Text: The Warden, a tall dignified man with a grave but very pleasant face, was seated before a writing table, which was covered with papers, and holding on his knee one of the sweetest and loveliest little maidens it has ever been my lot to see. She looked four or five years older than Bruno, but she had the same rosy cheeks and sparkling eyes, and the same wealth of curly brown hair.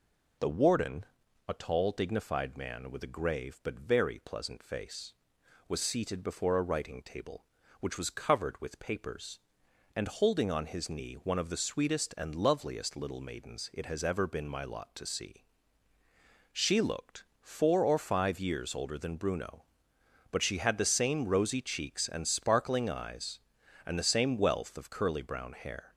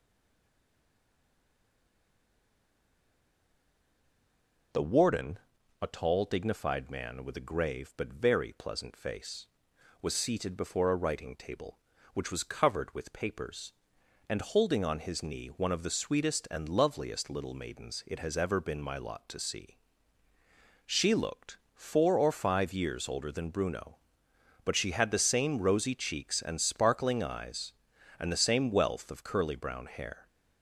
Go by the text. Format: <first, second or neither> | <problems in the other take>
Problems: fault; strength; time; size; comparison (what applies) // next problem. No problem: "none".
first | stays silent before the first word; strong; until 4.7 s; 4.7 s long // pauses between "looked" and "four"; slight; at 21.5 s; 0.16 s long; slight in the first